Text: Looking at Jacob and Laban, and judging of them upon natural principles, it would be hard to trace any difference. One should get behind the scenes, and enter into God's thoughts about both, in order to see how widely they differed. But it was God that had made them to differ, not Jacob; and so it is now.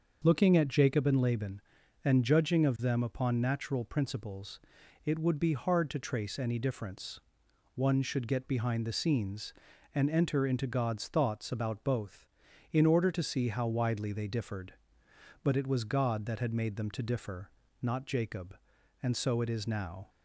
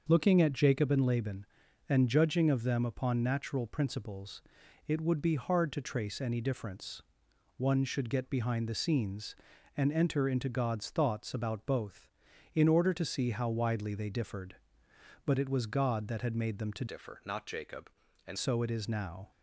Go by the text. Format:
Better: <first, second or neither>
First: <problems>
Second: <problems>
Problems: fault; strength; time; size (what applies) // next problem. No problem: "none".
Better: first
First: starts louder than the rest; until 1.2 s; 6 dB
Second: starts louder than the rest; until 1.1 s; 6 dB // changes voice from "differ" to "and"; from 16.8 to 18.3 s; 1.5 s long